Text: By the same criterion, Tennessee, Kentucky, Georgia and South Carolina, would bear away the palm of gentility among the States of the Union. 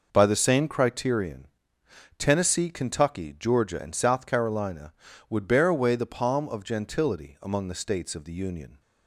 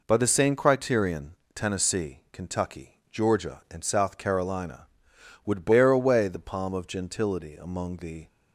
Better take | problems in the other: first | stops before "States of the Union"; at 8.2 s

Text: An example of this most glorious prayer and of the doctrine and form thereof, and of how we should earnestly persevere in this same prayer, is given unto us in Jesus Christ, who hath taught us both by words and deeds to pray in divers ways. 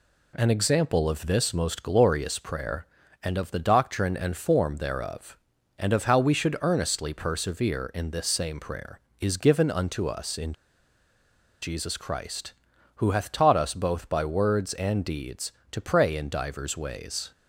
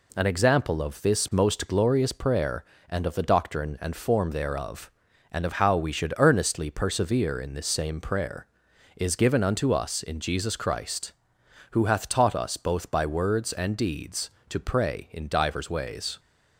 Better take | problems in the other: second | pauses between "in" and "Jesus"; at 10.5 s; 1.0 s long

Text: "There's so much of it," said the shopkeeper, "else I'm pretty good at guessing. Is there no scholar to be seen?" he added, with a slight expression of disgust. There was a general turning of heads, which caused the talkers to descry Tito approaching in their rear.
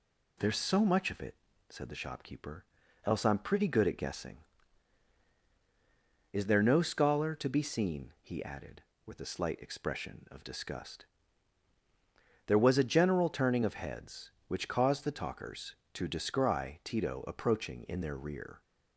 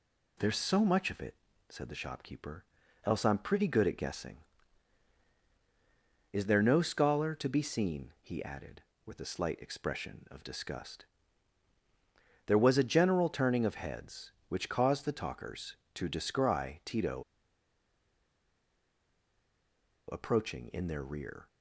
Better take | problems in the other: first | pauses between "Tito" and "approaching"; strong; at 17.2 s; 2.8 s long

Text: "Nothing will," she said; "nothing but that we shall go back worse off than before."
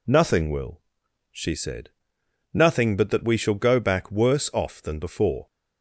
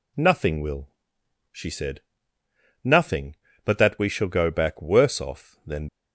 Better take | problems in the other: first | stops before "before"; at 5.8 s

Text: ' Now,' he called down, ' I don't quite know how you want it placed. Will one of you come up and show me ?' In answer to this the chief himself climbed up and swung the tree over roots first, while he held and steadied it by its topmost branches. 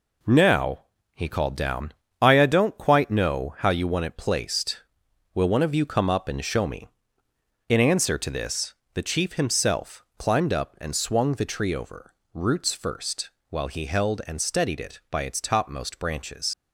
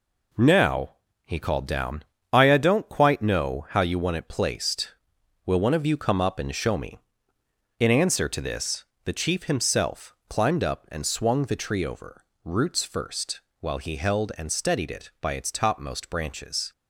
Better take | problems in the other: second | pauses between "this" and "the"; slight; at 8.7 s; 0.18 s long; slight in the second // pauses between "over" and "roots"; slight; at 12.1 s; 0.22 s long; slight in the second // leaves "branches" unfinished; at 16.5 s; 75 ms

